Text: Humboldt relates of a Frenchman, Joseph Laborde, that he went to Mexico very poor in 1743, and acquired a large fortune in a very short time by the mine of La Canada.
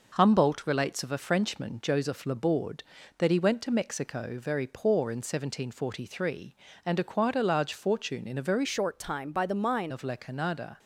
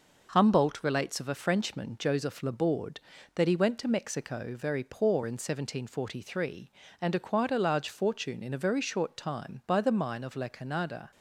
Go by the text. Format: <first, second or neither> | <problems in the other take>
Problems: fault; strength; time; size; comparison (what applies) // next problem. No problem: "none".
second | changes voice from "short" to "mine"; from 8.6 to 9.9 s; 1.3 s long